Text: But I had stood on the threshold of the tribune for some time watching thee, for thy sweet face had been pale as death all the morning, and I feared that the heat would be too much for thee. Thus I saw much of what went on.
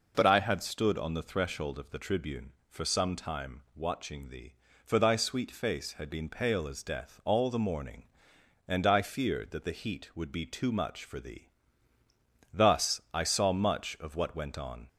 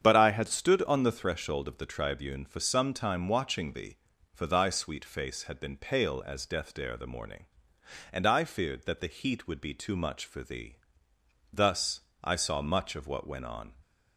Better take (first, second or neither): first